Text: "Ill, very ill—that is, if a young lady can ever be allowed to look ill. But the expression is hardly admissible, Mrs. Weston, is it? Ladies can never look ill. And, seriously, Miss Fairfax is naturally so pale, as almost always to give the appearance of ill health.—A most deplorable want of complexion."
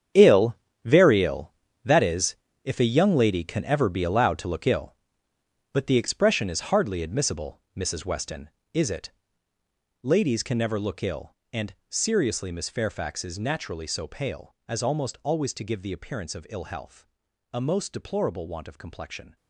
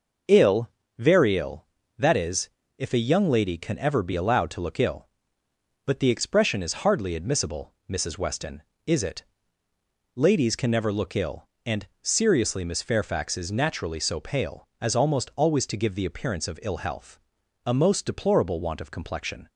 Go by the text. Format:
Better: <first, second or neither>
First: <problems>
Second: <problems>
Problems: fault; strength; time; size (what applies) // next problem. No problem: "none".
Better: second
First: gets quieter; strong; throughout; 13.5 dB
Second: none